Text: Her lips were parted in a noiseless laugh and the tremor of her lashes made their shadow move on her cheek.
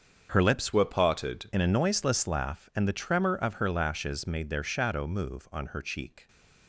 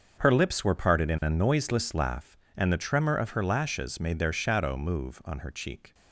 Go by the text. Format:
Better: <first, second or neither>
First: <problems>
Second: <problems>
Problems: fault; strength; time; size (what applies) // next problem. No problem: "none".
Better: second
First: starts louder than the rest; until 1.3 s; 6.5 dB // changes voice from "were" to "parted"; from 0.7 to 1.5 s; 0.8 s long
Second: starts louder than the rest; until 1.1 s; 6.5 dB